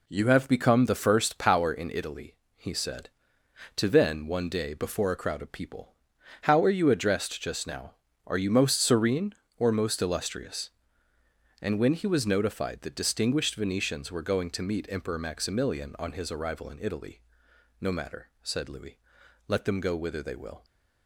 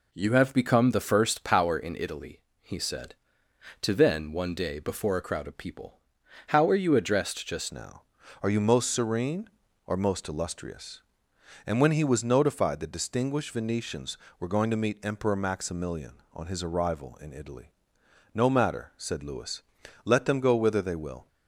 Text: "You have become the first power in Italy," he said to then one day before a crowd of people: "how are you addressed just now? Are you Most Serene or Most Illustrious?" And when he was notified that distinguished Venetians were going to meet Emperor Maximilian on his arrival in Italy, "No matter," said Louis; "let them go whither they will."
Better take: first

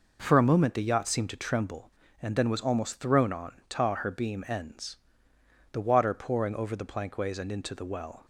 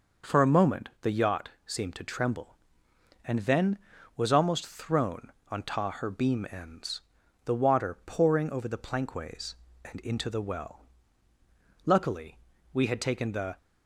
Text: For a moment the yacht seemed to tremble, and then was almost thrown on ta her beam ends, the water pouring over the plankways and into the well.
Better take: first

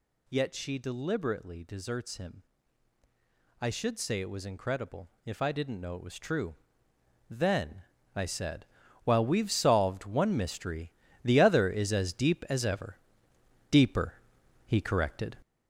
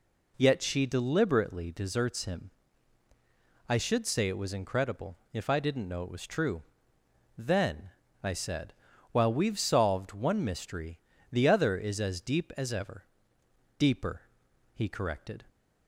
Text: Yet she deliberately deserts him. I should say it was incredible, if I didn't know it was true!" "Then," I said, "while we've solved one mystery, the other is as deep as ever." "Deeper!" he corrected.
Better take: second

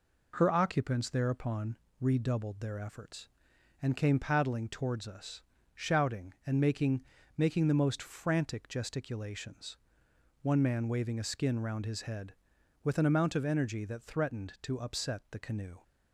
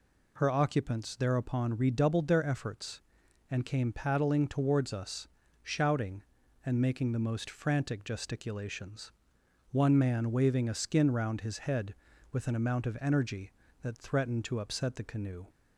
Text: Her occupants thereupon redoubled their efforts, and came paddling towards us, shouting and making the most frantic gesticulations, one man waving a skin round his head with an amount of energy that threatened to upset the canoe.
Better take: second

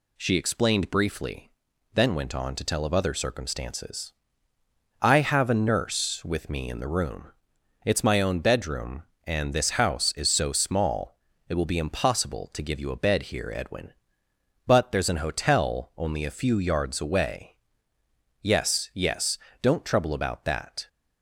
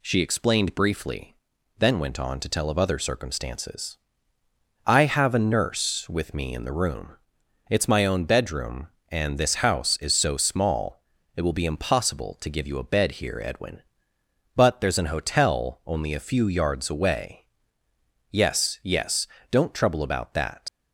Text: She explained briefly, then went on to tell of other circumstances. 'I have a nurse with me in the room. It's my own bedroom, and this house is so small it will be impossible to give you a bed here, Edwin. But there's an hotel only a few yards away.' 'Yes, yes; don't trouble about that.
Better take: first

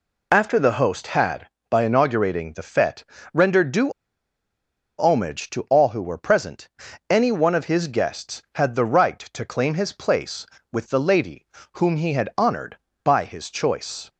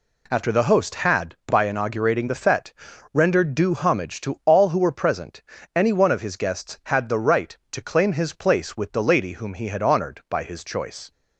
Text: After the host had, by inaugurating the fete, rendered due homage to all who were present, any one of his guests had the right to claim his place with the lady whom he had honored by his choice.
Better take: second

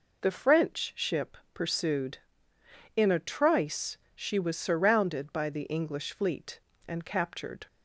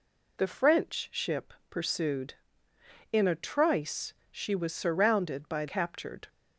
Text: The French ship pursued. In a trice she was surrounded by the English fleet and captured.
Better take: first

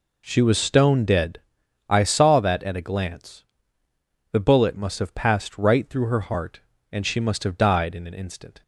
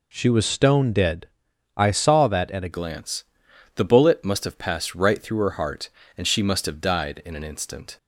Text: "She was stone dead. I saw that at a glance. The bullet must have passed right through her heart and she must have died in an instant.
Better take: first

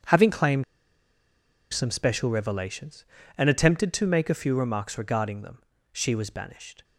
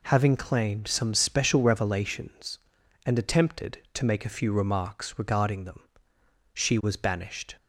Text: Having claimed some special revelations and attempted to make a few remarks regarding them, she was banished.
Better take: second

